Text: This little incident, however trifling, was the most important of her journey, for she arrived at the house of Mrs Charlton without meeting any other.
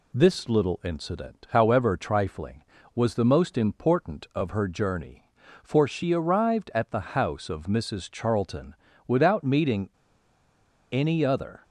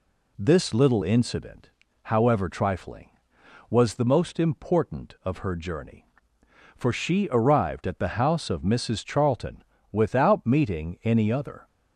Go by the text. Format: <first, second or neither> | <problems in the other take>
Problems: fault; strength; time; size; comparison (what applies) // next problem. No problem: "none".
second | pauses between "Charlton" and "without"; slight; at 8.7 s; 0.34 s long; slight in the second // pauses between "meeting" and "any"; at 9.8 s; 1.0 s long